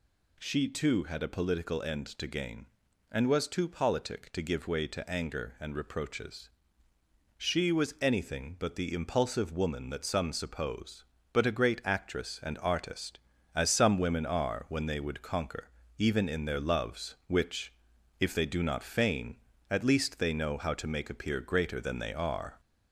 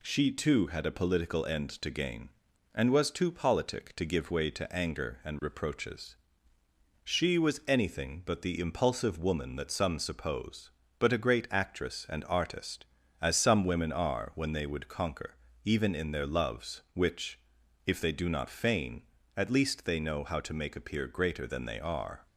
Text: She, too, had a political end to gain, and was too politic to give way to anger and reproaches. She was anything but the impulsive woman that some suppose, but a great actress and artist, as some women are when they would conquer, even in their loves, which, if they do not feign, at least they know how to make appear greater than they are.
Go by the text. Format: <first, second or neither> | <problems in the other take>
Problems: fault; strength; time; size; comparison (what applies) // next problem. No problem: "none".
second | gets louder; slight; throughout; 2.5 dB